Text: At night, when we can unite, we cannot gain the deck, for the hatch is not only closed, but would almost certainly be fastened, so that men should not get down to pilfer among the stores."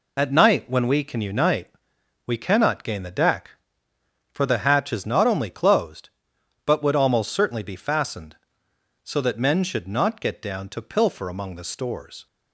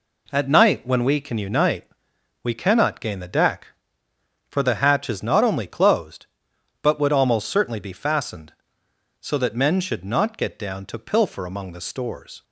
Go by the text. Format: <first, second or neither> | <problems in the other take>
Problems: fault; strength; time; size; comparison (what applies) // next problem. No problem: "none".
second | loses the start of "At"; at 0.1 s; 60 ms